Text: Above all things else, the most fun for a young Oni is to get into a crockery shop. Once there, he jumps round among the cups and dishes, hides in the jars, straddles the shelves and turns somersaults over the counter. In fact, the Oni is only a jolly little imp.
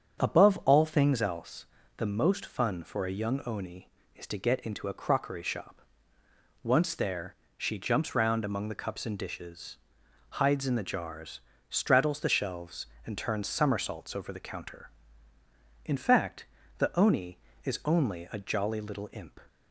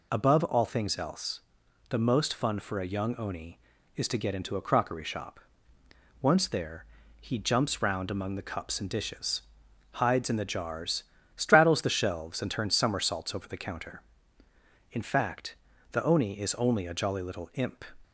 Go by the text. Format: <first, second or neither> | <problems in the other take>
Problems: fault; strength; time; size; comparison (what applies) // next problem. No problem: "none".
second | starts louder than the rest; strong; until 1.2 s; 7.5 dB // says "she" for "he"; at 7.5 s